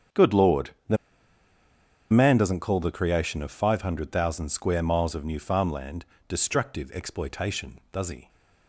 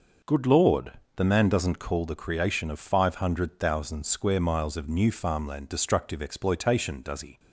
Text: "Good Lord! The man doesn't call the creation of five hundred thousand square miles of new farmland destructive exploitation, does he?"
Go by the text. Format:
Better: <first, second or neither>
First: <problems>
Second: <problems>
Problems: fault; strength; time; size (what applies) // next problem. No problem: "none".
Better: second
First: starts louder than the rest; strong; until 2.4 s; 8 dB // pauses between "The" and "man"; at 0.9 s; 1.1 s long // pauses between "farmland" and "destructive"; slight; at 6.0 s; 0.24 s long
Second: none